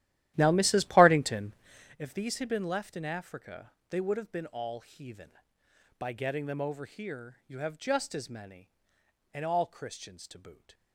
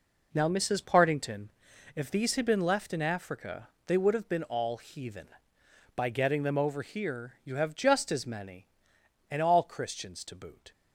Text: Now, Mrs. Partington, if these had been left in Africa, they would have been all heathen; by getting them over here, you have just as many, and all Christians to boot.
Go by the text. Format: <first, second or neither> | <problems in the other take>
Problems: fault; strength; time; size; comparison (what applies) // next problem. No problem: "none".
second | starts louder than the rest; strong; until 2.0 s; 13.5 dB